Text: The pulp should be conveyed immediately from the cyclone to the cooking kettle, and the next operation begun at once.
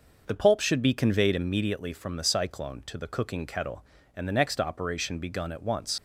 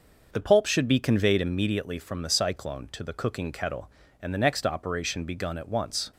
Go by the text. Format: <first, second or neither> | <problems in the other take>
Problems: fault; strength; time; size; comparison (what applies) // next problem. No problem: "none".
second | leaves "once" unfinished; at 5.9 s; 80 ms